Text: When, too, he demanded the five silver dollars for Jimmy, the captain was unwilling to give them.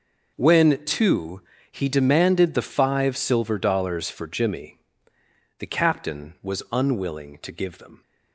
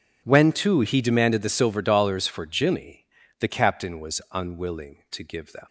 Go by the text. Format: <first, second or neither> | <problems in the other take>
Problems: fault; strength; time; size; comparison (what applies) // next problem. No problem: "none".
first | skips "five"; at 1.4 s